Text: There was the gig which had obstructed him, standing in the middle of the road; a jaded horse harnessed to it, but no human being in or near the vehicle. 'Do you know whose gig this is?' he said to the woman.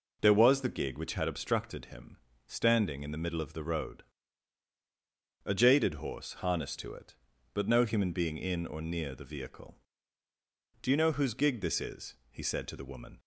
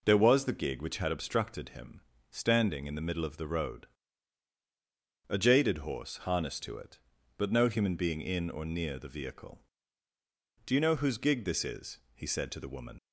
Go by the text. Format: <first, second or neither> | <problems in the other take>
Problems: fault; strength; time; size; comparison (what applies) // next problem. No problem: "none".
first | leaves "woman" unfinished; at 12.9 s; 45 ms